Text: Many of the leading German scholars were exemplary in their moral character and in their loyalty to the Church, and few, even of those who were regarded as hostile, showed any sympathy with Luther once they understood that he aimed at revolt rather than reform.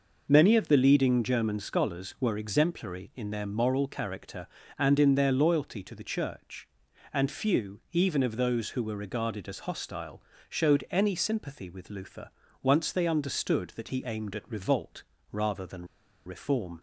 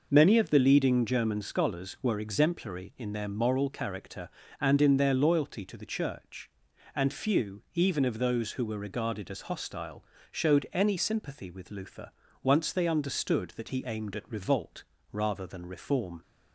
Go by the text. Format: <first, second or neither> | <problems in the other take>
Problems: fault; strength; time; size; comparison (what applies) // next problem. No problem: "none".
second | pauses between "Luther" and "once"; slight; at 12.3 s; 0.32 s long; slight in the second // pauses between "revolt" and "rather"; slight; at 15.0 s; 0.28 s long; slight in the second // pauses between "than" and "reform"; at 15.8 s; 0.41 s long